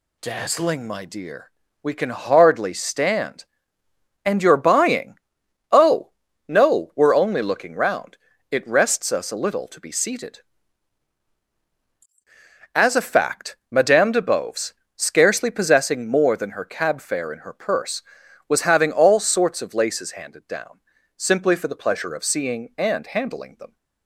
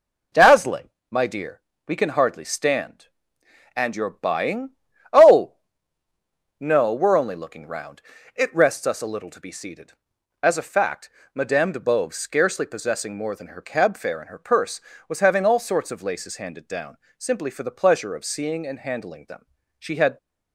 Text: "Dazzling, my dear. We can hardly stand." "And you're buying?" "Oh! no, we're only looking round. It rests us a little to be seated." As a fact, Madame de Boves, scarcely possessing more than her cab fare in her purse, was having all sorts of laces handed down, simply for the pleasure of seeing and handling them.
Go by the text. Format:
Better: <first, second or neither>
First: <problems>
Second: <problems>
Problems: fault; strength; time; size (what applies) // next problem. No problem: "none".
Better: first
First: none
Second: goes on to say "She had"; slight; from 19.7 s on; 0.40 s long